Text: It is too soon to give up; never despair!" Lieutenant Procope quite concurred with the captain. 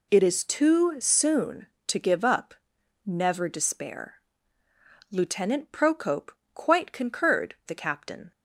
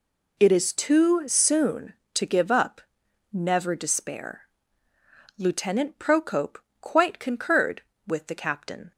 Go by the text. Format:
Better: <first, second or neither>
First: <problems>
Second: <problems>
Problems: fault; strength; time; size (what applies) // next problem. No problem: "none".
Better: second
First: pauses between "Procope" and "quite"; slight; at 6.3 s; 0.24 s long // skips "with"; at 7.6 s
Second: pauses between "Procope" and "quite"; slight; at 6.5 s; 0.24 s long